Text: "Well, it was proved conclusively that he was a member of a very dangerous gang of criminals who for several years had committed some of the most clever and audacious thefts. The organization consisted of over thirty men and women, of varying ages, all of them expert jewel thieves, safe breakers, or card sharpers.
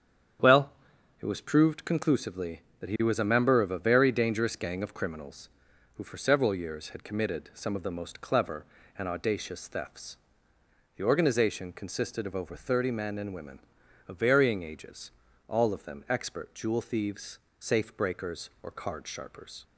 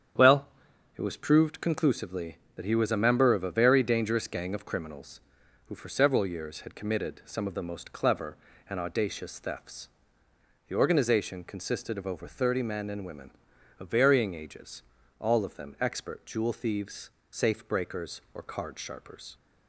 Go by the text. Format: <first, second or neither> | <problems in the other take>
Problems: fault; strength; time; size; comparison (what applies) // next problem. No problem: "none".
neither | starts louder than the rest; strong; the same in both